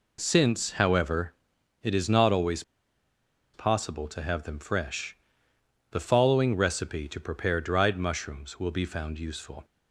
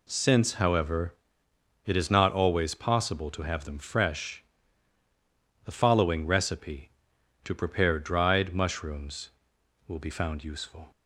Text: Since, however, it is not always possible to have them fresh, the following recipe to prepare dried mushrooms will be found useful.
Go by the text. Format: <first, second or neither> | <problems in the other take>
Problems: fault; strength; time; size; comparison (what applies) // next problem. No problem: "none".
second | pauses between "always" and "possible"; noticeable; at 2.6 s; 0.92 s long